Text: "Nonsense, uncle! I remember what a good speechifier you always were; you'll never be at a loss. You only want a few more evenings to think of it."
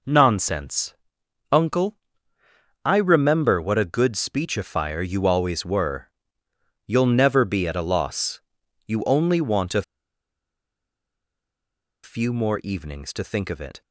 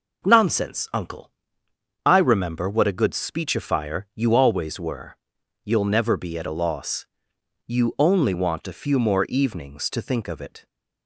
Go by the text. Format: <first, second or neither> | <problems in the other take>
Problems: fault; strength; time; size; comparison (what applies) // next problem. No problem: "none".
second | pauses between "a" and "few"; strong; at 9.8 s; 2.2 s long